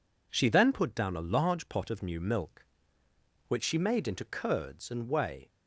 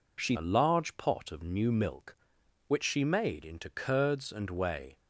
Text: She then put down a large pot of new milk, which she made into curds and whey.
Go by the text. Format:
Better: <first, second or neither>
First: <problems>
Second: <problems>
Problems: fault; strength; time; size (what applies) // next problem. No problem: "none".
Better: first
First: none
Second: skips "then put down"; at 0.3 s